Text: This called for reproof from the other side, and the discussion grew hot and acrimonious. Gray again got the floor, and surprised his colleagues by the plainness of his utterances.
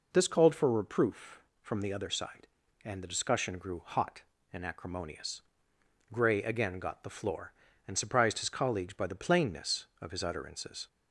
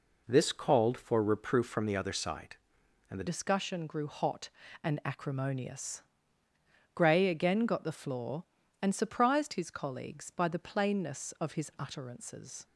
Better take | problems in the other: first | changes voice at "discussion"; from 3.2 s on; 9.4 s long

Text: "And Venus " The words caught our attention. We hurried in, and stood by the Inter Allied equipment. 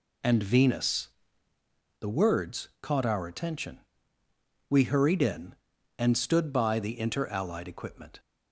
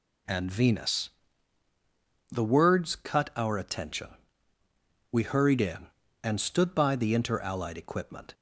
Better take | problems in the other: first | says "cut" for "caught"; at 2.9 s

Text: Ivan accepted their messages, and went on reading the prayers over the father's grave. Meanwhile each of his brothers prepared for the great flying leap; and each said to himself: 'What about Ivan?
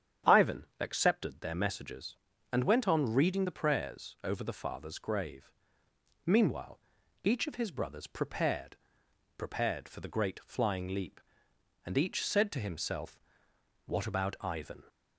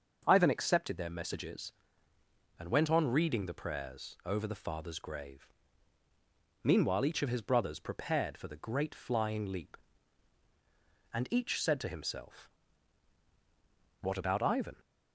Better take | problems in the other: second | starts louder than the rest; strong; until 1.4 s; 9 dB; also in the second // pauses between "Ivan" and "accepted"; slight; at 0.6 s; 0.16 s long // pauses between "Meanwhile" and "each"; noticeable; at 6.7 s; 0.46 s long // says "prepared" twice; at 9.3 s

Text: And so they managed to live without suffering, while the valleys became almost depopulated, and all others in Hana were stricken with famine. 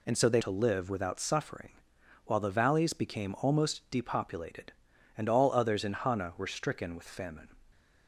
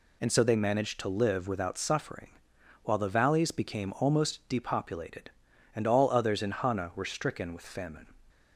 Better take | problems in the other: second | skips "managed"; at 0.4 s

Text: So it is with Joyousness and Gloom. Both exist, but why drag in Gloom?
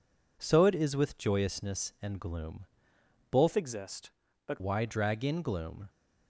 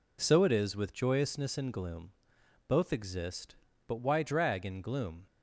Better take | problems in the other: second | changes voice from "exist" to "but"; from 3.5 to 4.6 s; 1.1 s long

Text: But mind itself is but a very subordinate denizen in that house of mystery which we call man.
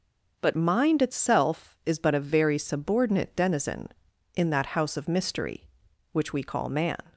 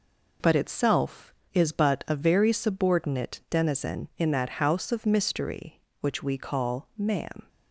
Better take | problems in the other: first | skips "mind"; at 0.5 s

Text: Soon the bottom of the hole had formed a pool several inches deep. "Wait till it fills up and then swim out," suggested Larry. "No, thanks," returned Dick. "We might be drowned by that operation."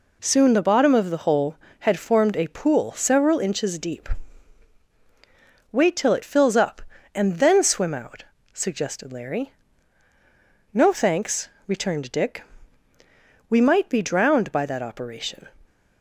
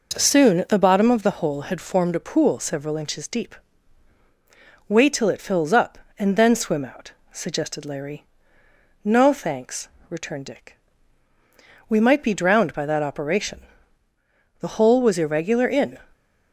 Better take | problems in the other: first | goes on to say "The hole was irregular in"; from 14.5 s on; 1.3 s long

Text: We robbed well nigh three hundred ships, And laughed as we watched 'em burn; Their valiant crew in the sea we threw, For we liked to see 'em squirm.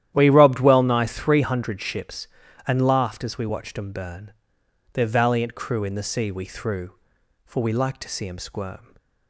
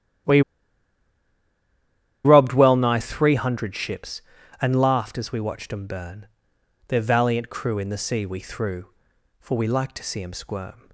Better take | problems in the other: first | starts louder than the rest; strong; until 3.1 s; 11.5 dB; strong in the first // pauses between "We" and "robbed"; strong; at 0.4 s; 1.8 s long

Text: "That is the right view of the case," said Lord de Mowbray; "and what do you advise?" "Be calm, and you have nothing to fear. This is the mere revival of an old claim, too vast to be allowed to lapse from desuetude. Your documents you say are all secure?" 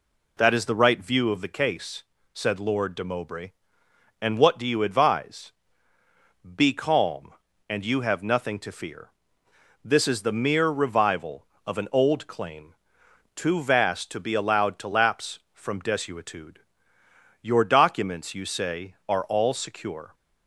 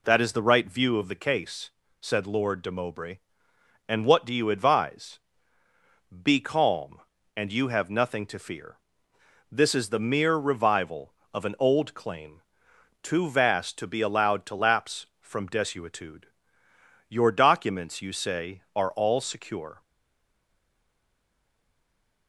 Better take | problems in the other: first | stays silent after the last word; from 19.8 s on; 2.4 s long

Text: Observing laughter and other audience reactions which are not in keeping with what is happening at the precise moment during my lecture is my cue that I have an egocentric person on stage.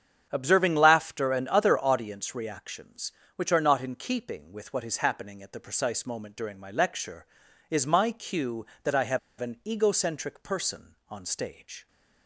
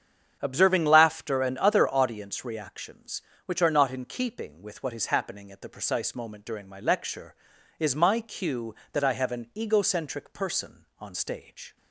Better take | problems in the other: second | starts louder than the rest; strong; until 1.3 s; 8 dB; strong in the second // pauses between "have" and "an"; slight; at 9.1 s; 0.21 s long

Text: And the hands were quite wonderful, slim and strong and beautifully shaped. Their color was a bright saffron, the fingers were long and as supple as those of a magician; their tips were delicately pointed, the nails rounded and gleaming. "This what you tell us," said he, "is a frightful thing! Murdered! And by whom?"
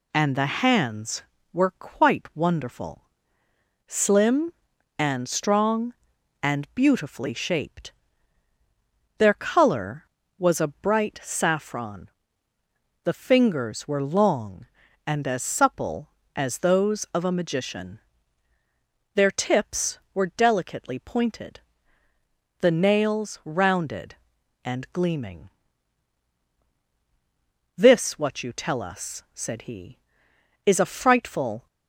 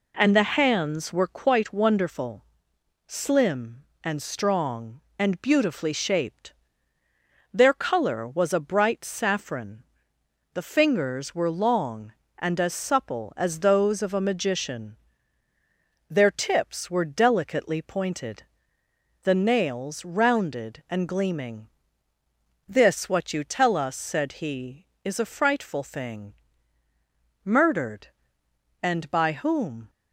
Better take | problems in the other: second | stops before "thing Murdered And by whom"; at 31.6 s

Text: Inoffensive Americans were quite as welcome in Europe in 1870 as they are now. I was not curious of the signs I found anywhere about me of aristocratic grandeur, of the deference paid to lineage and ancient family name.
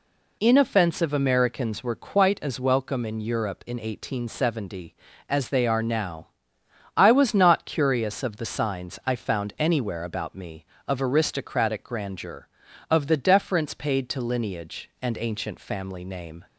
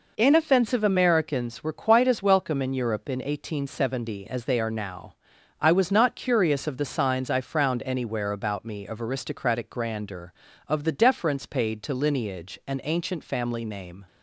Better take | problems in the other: first | says "frowned" for "found"; at 7.3 s

